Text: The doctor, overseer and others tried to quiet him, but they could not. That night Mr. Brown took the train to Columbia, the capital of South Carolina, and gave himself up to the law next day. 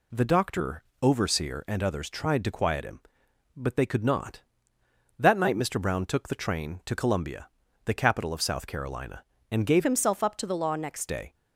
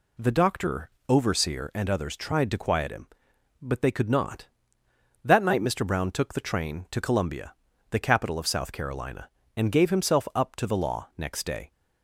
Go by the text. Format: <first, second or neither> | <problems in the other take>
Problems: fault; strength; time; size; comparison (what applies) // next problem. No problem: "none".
second | changes voice from "himself" to "next"; from 9.8 to 11.0 s; 1.2 s long